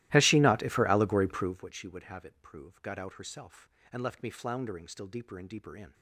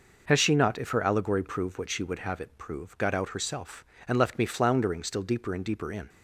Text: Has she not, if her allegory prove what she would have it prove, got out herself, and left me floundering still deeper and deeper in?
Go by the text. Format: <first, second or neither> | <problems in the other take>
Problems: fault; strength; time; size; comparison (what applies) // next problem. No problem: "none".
second | starts louder than the rest; strong; until 1.7 s; 16.5 dB